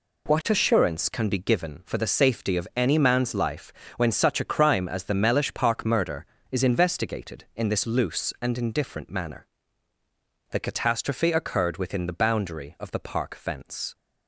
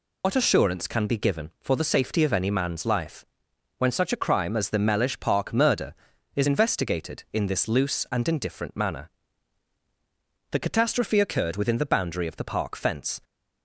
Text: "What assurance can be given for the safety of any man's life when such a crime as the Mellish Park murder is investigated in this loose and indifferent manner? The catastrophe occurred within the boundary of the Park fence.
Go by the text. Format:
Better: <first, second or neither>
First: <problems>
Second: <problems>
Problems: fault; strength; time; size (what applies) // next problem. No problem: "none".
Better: first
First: pauses between "life" and "when"; slight; at 3.7 s; 0.24 s long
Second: loses the start of "What"; at 0.2 s; 95 ms // pauses between "life" and "when"; noticeable; at 3.2 s; 0.54 s long